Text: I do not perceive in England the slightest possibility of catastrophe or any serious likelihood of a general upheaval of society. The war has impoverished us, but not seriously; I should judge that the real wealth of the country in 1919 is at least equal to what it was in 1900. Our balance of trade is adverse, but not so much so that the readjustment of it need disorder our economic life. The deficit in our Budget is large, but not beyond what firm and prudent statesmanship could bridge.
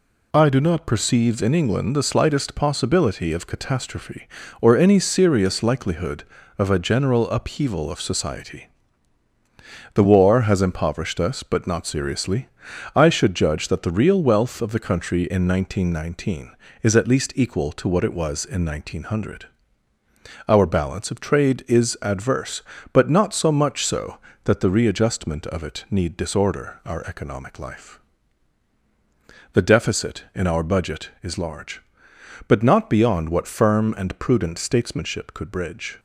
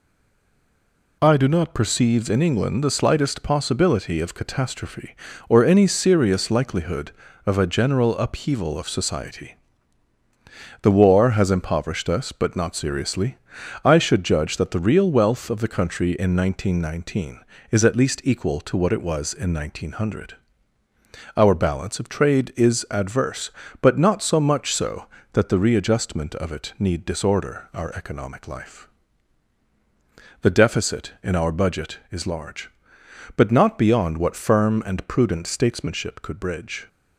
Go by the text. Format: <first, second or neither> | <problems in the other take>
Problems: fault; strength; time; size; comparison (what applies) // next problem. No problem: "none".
first | stays silent before the first word; noticeable; until 1.2 s; 1.2 s long